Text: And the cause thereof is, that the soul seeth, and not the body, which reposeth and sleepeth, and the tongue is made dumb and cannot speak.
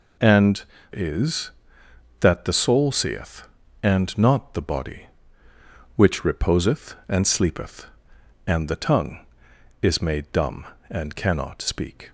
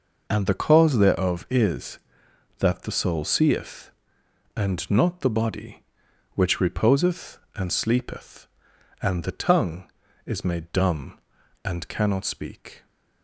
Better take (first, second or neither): second